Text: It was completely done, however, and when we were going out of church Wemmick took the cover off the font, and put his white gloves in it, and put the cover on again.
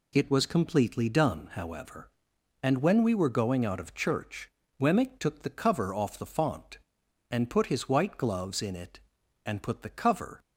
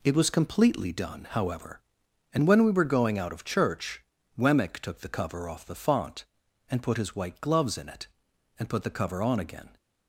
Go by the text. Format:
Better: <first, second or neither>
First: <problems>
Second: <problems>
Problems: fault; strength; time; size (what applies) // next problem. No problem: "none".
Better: second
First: pauses between "church" and "Wemmick"; slight; at 4.4 s; 0.32 s long // stops before "on again"; at 10.3 s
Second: pauses between "church" and "Wemmick"; slight; at 4.0 s; 0.36 s long